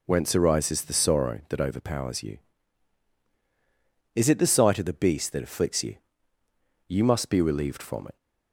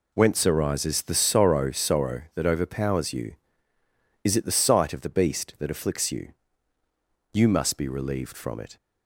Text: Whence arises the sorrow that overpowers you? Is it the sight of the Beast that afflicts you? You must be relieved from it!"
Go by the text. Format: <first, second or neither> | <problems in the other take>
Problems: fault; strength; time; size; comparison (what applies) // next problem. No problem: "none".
first | says "sorrow" twice; at 1.7 s